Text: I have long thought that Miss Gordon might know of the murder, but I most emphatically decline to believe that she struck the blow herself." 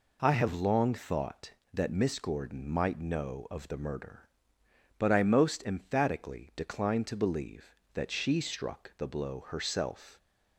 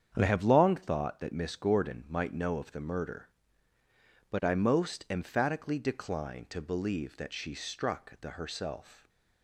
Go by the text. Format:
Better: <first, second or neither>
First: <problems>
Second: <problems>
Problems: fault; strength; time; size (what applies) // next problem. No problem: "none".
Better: first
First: none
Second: starts louder than the rest; strong; until 1.2 s; 8 dB // skips "blow"; at 8.3 s